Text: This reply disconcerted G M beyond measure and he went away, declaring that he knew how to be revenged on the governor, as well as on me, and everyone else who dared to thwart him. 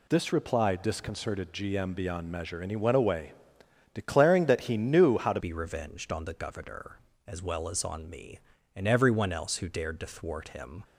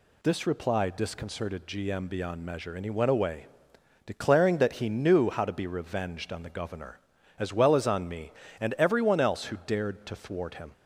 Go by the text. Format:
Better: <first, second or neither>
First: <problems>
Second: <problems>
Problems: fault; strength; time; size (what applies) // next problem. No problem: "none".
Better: second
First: changes voice at "be"; from 5.4 s on; 5.4 s long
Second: none